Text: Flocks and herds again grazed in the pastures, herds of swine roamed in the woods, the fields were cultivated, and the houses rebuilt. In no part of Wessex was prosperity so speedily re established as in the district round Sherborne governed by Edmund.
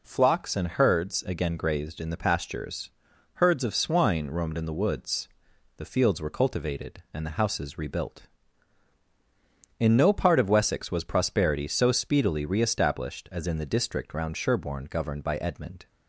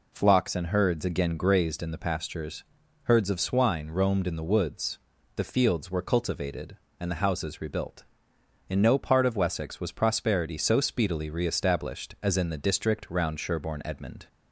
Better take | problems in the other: first | skips "governed by"; at 13.8 s

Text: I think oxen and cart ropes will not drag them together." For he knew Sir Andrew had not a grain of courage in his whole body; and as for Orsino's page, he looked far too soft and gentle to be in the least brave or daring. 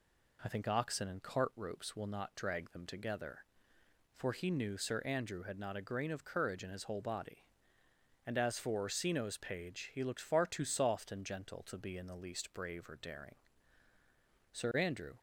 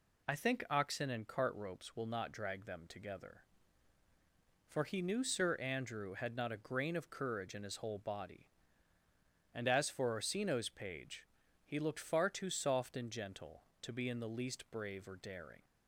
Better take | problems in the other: second | goes on to say "Sir Andrew"; noticeable; from 14.5 s on; 0.66 s long

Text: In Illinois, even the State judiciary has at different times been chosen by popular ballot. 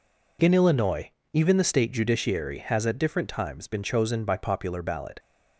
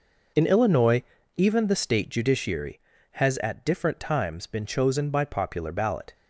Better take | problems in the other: neither | none

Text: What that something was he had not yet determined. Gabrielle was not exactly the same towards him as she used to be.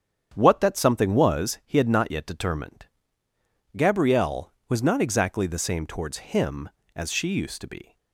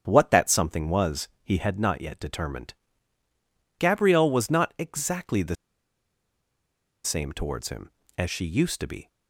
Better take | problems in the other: first | starts louder than the rest; strong; until 1.0 s; 8 dB; strong in the first // pauses between "was" and "he"; slight; at 1.2 s; 0.16 s long // pauses between "the" and "same"; strong; at 5.5 s; 1.4 s long

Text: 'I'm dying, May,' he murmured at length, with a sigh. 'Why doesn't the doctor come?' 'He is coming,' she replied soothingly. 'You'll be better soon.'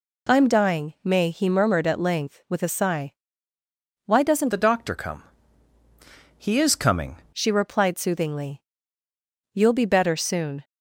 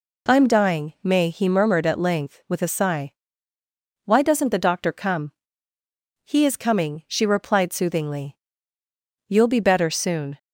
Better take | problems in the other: second | changes voice from "the" to "coming"; from 4.5 to 7.1 s; 2.6 s long

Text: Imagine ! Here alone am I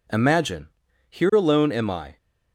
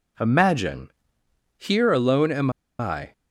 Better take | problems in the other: first | pauses between "am" and "I"; slight; at 2.4 s; 0.30 s long

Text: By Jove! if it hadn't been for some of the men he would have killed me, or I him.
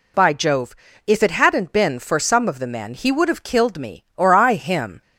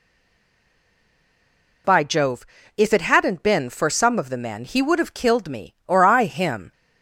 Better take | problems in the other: first | stays silent before the first word; noticeable; until 1.8 s; 1.8 s long

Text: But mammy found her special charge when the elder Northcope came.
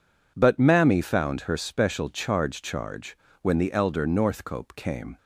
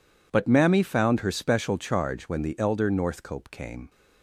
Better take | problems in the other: second | says "charge" twice; at 2.6 s

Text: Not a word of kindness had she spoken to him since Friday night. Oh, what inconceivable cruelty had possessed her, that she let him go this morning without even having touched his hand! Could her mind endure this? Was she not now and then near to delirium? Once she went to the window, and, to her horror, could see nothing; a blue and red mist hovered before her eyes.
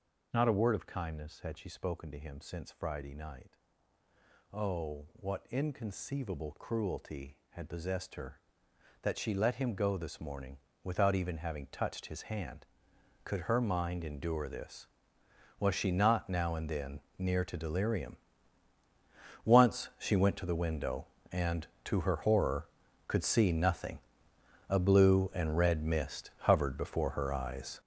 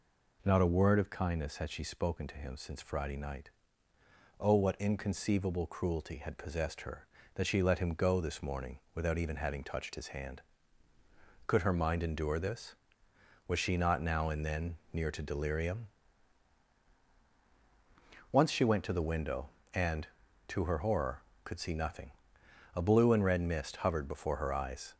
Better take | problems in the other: second | gets louder; strong; throughout; 10.5 dB // pauses between "morning" and "without"; slight; at 10.5 s; 0.26 s long; slight in the second // pauses between "then" and "near"; slight; at 16.9 s; 0.18 s long; slight in the second

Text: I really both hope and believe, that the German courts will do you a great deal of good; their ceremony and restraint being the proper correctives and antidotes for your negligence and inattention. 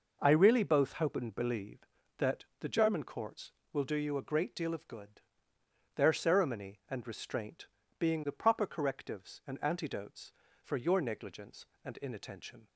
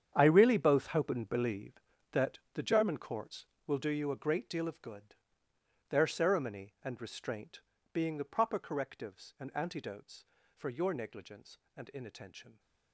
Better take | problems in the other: first | gets quieter; strong; throughout; 15 dB // pauses between "that" and "the"; slight; at 2.3 s; 0.16 s long; slight in the first // pauses between "restraint" and "being"; slight; at 7.6 s; 0.32 s long; slight in the first

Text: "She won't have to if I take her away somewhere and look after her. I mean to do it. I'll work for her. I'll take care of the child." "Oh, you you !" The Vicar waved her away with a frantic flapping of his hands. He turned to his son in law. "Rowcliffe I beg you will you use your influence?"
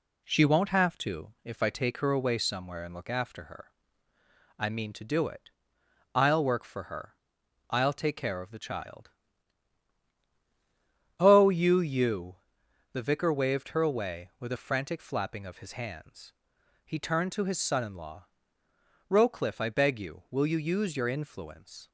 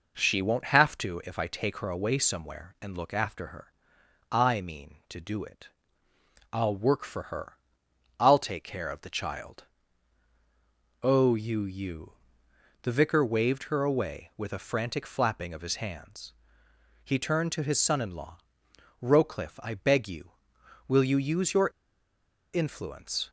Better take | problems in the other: first | pauses between "your" and "influence"; noticeable; at 21.6 s; 0.87 s long

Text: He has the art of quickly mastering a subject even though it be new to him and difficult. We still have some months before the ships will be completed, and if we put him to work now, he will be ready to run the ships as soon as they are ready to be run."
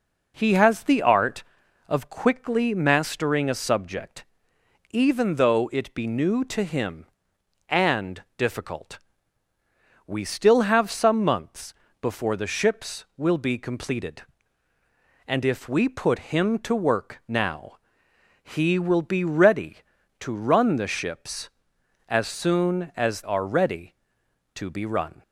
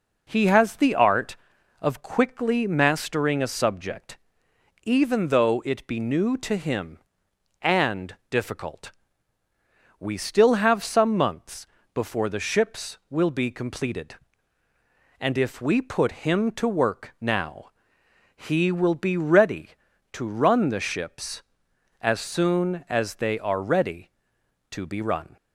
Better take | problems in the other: second | pauses between "subject" and "even"; noticeable; at 4.2 s; 0.64 s long; noticeable in the second // pauses between "months" and "before"; slight; at 11.7 s; 0.28 s long; slight in the second // skips "they"; at 23.2 s

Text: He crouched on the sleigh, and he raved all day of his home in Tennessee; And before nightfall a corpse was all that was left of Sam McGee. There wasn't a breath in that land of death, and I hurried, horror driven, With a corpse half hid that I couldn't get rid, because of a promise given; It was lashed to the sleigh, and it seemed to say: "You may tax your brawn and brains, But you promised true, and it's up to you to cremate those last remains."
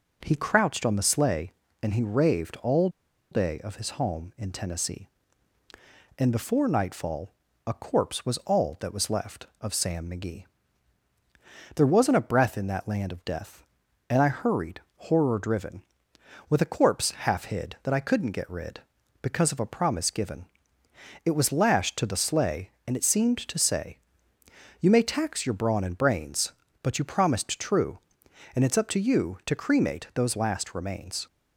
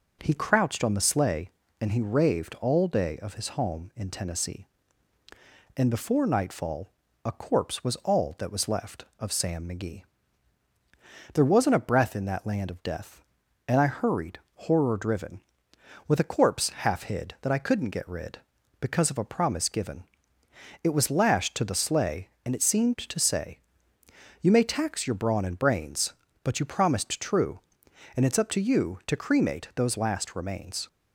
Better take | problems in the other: second | pauses between "all" and "day"; at 2.8 s; 0.43 s long // pauses between "nightfall" and "a"; slight; at 7.3 s; 0.34 s long; slight in the second

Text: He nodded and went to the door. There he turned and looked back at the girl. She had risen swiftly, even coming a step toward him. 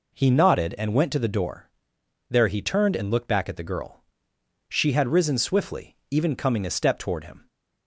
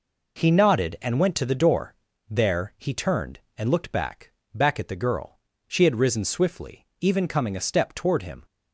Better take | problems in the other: first | says "back" twice; at 4.5 s

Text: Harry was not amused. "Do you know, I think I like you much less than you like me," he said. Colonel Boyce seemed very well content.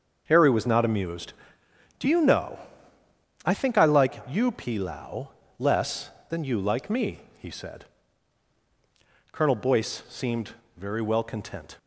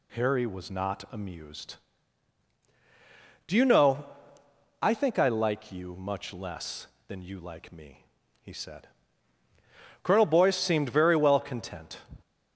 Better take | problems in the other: second | starts louder than the rest; until 1.2 s; 6.5 dB // says "pilau" for "much"; at 4.5 s // pauses between "seemed" and "very"; slight; at 10.5 s; 0.26 s long

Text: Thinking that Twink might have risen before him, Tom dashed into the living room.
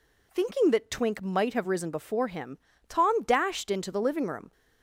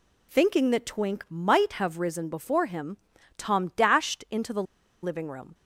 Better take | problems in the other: first | pauses between "the" and "living"; at 4.6 s; 0.39 s long

